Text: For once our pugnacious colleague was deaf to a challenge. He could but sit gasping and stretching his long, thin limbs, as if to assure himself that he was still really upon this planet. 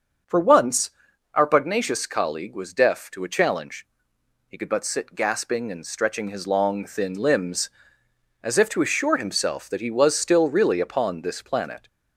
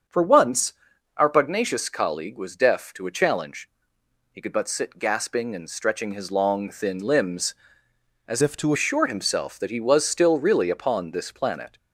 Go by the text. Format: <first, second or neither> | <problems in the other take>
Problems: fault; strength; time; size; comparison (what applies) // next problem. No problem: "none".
first | starts louder than the rest; strong; until 1.5 s; 7.5 dB; also in the first // pauses between "once" and "our"; at 0.7 s; 0.44 s long; also in the first // changes voice from "if" to "to"; from 8.4 to 8.7 s; 0.3 s long